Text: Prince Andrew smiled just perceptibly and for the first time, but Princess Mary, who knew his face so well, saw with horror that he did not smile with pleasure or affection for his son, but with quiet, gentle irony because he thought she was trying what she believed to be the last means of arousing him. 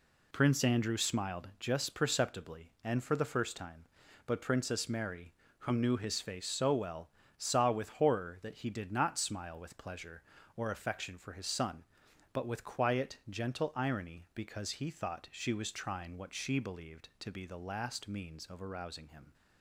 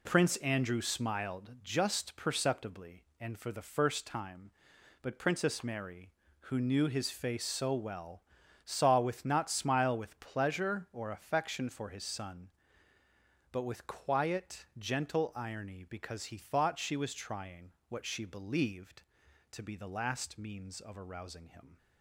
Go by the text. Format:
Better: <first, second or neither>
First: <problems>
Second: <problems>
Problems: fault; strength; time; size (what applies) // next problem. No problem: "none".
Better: first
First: none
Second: skips "horror that he did"; at 9.2 s // pauses between "trying" and "what"; slight; at 17.7 s; 0.16 s long